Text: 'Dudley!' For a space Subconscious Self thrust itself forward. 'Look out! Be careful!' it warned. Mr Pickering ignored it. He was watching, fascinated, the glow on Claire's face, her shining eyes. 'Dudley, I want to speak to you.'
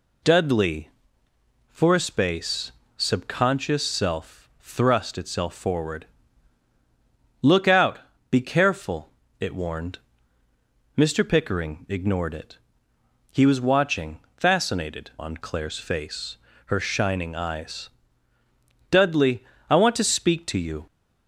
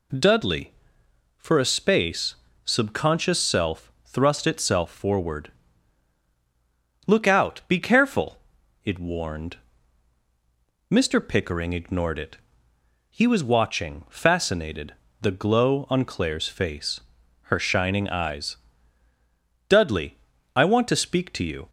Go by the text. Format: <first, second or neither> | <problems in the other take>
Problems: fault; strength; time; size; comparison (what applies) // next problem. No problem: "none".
second | pauses between "space" and "Subconscious"; slight; at 2.7 s; 0.26 s long; slight in the second // skips "the glow"; at 15.1 s